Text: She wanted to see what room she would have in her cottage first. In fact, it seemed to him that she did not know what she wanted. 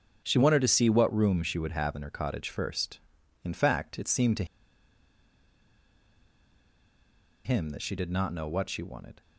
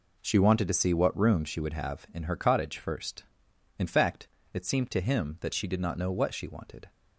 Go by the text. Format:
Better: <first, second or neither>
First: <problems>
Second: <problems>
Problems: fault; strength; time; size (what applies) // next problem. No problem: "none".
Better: second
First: starts louder than the rest; strong; until 1.2 s; 7.5 dB // pauses between "to" and "him"; strong; at 4.4 s; 3.0 s long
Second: none